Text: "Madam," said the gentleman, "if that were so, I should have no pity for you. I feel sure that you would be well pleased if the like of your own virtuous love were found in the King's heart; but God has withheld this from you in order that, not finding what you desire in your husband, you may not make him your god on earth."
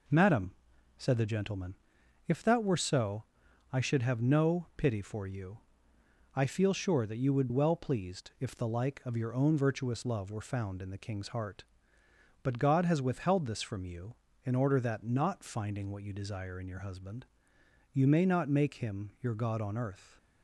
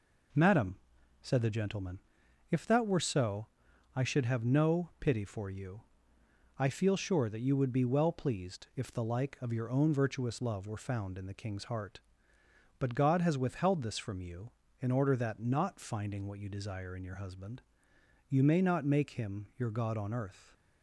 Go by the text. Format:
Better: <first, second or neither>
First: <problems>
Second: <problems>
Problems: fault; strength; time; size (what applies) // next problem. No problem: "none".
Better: second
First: skips "be"; at 7.4 s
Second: none